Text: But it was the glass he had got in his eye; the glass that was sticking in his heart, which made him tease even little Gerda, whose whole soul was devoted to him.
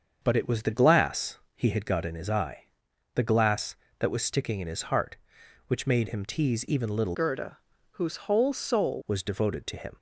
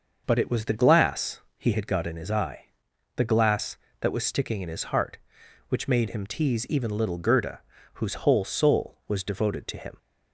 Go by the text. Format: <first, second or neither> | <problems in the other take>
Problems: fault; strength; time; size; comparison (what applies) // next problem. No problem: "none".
second | starts louder than the rest; until 1.2 s; 7 dB; noticeable in the second // pauses between "glass" and "he"; slight; at 1.3 s; 0.18 s long; slight in the second // changes voice from "Gerda" to "soul"; from 7.1 to 9.0 s; 1.9 s long